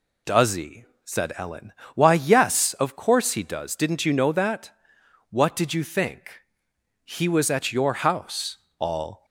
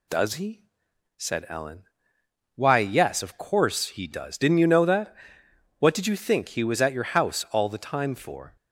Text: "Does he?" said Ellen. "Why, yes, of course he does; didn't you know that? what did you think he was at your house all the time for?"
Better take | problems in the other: second | pauses between "think" and "he"; noticeable; at 6.4 s; 0.62 s long // pauses between "house" and "all"; slight; at 8.5 s; 0.20 s long // stops before "the time for"; at 9.2 s

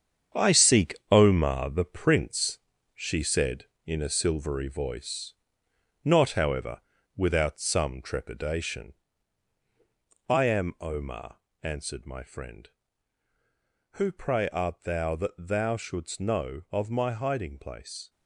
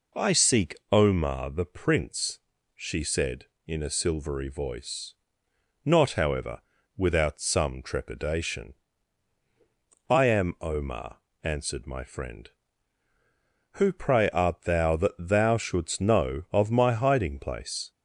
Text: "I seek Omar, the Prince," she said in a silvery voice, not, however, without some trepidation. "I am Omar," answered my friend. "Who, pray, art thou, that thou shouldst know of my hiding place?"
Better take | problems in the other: second | gets quieter; strong; throughout; 9.5 dB // pauses between "seek" and "Omar"; slight; at 0.9 s; 0.16 s long; slight in the second

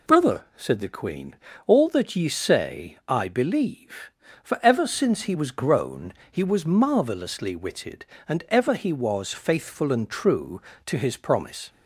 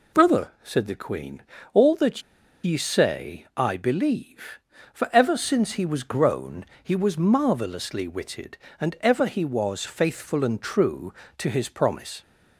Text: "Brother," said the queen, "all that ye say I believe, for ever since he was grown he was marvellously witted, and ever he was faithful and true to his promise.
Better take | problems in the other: first | pauses between "that" and "ye"; at 2.2 s; 0.41 s long // pauses between "grown" and "he"; slight; at 6.6 s; 0.18 s long; slight in the first

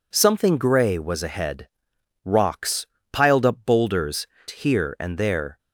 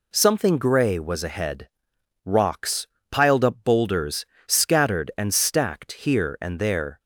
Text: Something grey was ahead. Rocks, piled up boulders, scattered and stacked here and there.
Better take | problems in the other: second | skips "scattered and stacked"; at 4.3 s

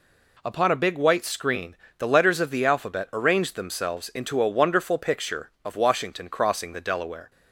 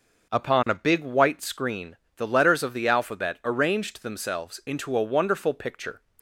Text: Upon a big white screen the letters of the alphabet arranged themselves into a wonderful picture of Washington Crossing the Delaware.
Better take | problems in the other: first | pauses between "screen" and "the"; slight; at 1.9 s; 0.18 s long; slight in the first // stops before "of Washington Crossing the Delaware"; at 6.1 s

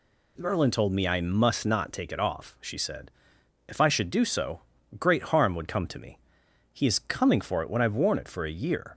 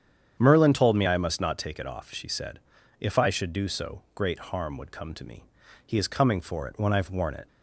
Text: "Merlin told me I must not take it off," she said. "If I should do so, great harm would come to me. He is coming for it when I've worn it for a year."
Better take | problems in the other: first | starts louder than the rest; strong; until 1.4 s; 8.5 dB // stops before "for a year"; at 7.4 s

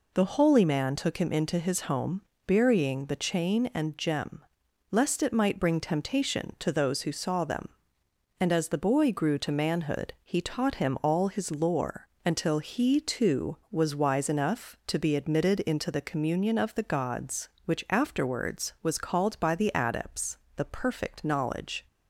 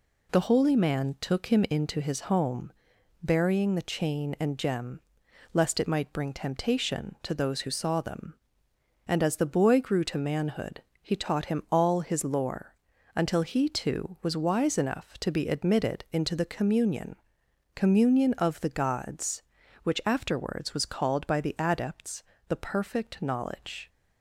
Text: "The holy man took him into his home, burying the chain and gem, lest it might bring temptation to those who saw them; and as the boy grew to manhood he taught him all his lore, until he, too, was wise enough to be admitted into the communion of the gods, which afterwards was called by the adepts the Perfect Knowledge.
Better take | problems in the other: first | pauses between "manhood" and "he"; slight; at 10.8 s; 0.18 s long // says "communion" twice; at 17.7 s // pauses between "adepts" and "the"; slight; at 22.2 s; 0.24 s long; slight in the first

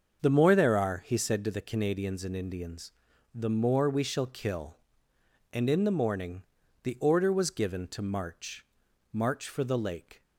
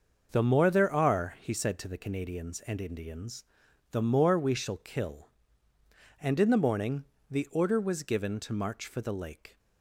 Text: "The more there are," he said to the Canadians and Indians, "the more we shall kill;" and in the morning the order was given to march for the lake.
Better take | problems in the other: second | starts louder than the rest; until 1.3 s; 6.5 dB; also in the second // pauses between "morning" and "the"; at 6.4 s; 0.40 s long; slight in the second // says "march" twice; at 9.1 s

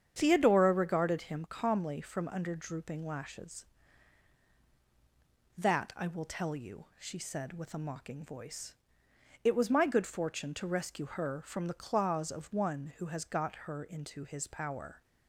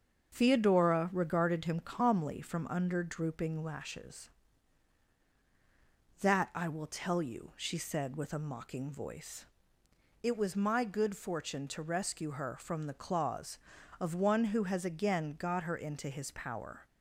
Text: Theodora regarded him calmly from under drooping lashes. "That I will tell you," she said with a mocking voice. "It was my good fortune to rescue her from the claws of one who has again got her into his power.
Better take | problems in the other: second | starts louder than the rest; strong; until 1.1 s; 8 dB; also in the second // skips "again"; at 13.2 s

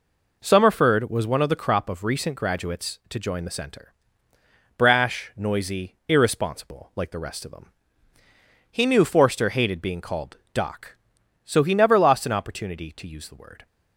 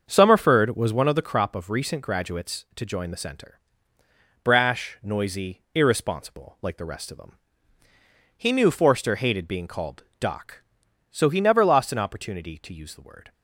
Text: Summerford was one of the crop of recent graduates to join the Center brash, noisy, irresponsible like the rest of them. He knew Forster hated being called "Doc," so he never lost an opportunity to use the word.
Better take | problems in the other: first | starts louder than the rest; until 1.3 s; 6.5 dB // pauses between "Center" and "brash"; noticeable; at 3.5 s; 0.86 s long; noticeable in the first // pauses between "called" and "Doc"; slight; at 10.0 s; 0.16 s long; slight in the first

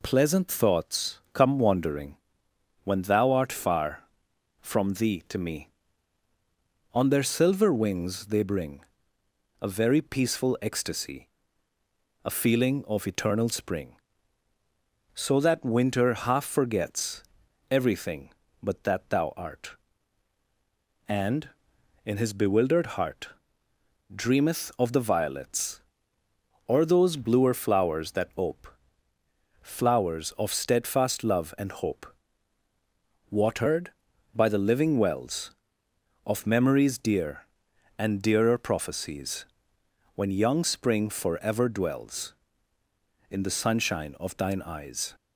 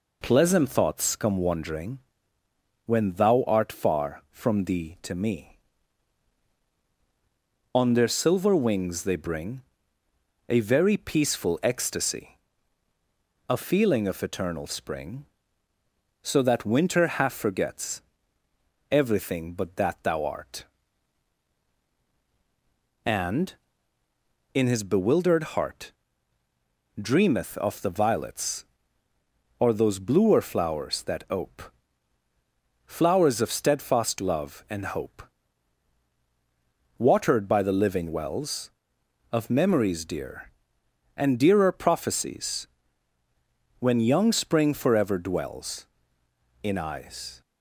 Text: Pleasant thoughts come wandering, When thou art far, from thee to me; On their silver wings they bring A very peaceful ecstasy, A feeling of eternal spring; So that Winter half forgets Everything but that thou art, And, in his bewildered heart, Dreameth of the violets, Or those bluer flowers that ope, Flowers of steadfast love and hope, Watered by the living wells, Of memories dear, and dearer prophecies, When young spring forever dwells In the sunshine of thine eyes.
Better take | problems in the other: first | pauses between "bring" and "A"; noticeable; at 9.6 s; 0.86 s long; noticeable in the first // pauses between "forgets" and "Everything"; noticeable; at 18.0 s; 0.90 s long; noticeable in the first // skips "the sunshine of thine"; at 46.7 s

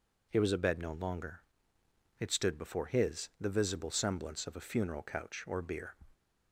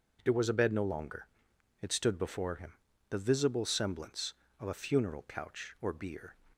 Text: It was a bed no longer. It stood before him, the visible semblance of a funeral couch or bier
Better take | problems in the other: second | says "his" for "him"; at 2.8 s

